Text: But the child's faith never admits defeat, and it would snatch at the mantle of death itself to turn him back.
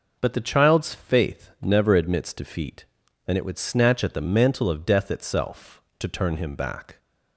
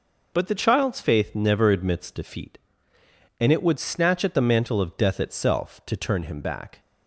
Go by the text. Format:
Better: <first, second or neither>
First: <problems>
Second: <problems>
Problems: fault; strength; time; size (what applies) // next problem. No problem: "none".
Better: neither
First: none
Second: none